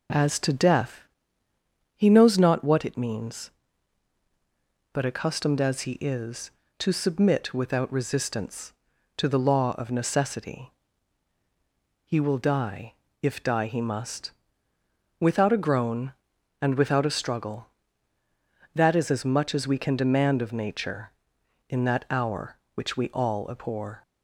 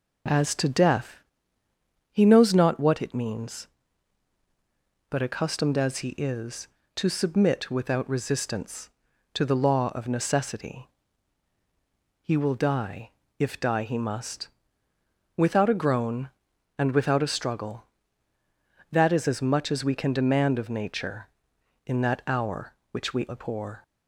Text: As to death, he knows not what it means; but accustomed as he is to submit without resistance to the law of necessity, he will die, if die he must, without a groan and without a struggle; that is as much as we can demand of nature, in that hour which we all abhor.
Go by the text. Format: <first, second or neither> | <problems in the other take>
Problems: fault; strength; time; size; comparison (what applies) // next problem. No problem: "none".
first | skips "all"; at 23.2 s